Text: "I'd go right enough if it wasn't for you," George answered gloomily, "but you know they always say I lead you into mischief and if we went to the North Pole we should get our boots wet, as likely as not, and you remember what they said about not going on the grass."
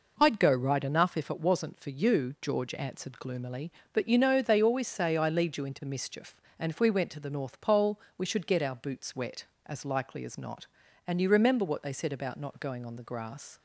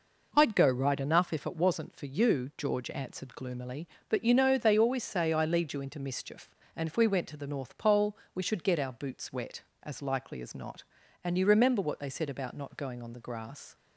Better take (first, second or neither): neither